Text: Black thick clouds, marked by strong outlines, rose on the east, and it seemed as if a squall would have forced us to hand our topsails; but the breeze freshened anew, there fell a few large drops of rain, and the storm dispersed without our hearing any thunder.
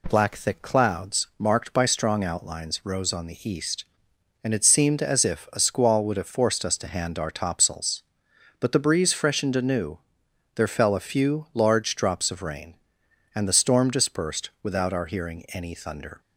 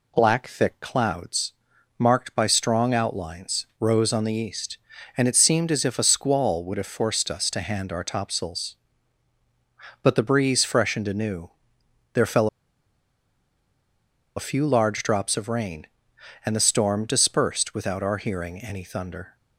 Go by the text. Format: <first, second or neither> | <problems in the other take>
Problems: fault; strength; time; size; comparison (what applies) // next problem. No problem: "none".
first | pauses between "fell" and "a"; strong; at 12.4 s; 1.8 s long